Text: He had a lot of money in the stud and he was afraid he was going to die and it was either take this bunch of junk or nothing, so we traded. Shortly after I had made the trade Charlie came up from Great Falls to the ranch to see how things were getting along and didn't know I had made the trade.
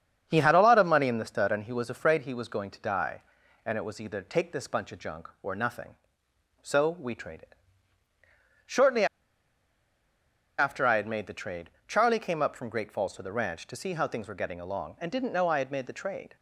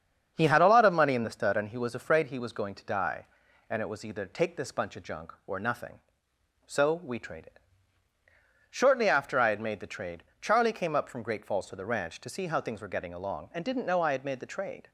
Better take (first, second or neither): second